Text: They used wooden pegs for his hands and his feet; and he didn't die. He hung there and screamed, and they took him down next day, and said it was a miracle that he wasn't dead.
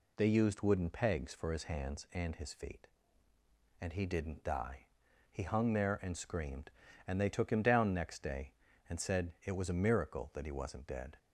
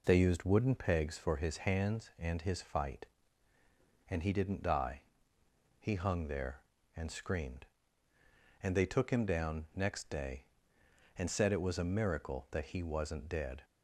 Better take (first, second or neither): first